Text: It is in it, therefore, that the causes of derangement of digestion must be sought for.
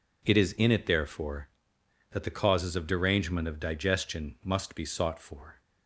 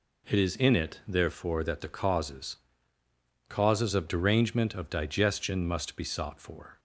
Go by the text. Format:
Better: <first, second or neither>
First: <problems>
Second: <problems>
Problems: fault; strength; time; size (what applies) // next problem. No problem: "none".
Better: first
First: none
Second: says "causes" twice; at 3.4 s